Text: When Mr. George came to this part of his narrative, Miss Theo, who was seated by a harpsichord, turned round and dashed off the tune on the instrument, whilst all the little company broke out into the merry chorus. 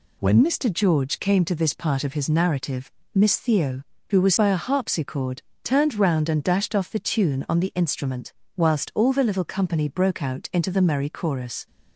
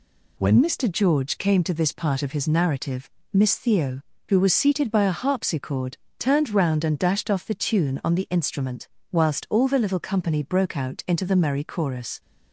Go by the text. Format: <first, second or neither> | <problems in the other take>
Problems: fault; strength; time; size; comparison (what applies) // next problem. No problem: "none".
second | skips "seated"; at 4.3 s